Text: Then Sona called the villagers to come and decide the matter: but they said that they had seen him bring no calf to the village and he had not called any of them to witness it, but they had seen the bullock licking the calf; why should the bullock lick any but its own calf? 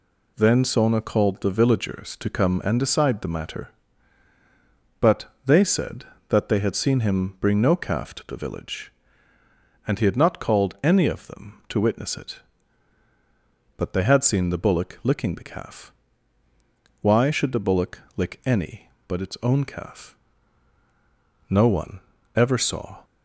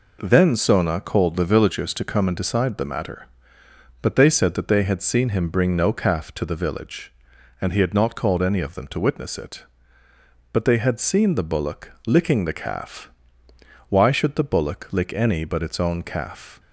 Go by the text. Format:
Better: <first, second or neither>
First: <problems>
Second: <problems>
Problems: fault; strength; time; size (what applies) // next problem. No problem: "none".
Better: second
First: pauses between "but" and "they"; slight; at 5.2 s; 0.20 s long // pauses between "bullock" and "lick"; slight; at 17.9 s; 0.16 s long // goes on to say "No one ever saw"; from 21.4 s on; 1.5 s long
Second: none